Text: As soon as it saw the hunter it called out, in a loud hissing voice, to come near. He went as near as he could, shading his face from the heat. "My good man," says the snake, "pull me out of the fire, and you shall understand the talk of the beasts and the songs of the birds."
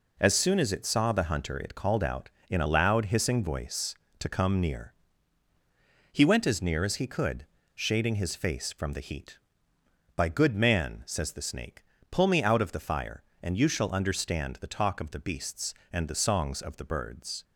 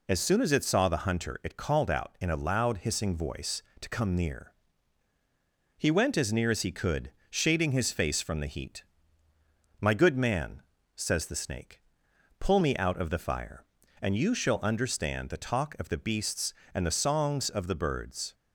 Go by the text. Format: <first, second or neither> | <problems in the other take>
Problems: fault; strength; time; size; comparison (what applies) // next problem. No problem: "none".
second | says "By" for "My"; at 10.1 s